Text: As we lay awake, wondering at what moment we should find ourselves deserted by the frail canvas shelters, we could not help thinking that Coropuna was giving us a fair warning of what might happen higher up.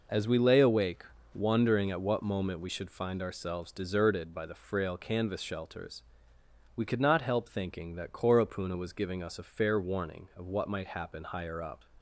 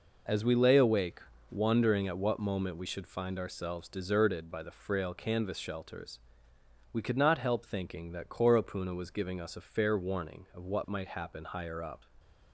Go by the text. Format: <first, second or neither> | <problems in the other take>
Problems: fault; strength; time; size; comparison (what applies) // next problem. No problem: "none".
neither | none